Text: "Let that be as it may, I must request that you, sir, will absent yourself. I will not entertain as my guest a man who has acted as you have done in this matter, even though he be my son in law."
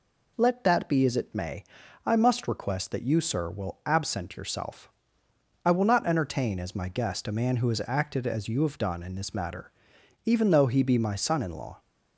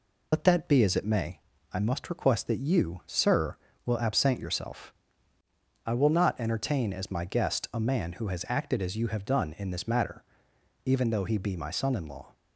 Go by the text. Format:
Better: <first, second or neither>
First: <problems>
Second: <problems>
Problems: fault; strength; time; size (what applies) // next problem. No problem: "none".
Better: first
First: none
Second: loses the start of "Let"; at 0.3 s; 55 ms